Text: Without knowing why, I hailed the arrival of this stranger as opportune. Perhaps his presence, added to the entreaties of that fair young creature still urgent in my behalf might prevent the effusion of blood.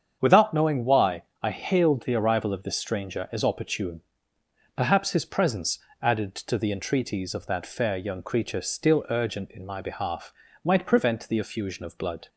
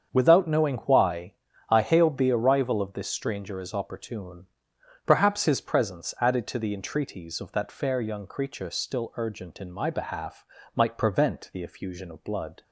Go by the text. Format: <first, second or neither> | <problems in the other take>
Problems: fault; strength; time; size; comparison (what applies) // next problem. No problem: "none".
neither | starts louder than the rest; strong; the same in both // pauses between "behalf" and "might"; slight; the same in both